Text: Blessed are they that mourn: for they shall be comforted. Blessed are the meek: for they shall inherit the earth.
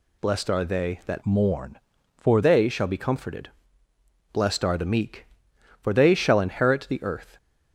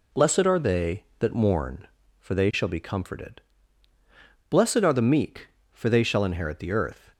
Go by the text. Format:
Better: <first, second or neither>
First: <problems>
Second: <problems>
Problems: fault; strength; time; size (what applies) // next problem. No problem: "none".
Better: second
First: changes voice from "mourn" to "for"; from 1.2 to 2.4 s; 1.2 s long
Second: none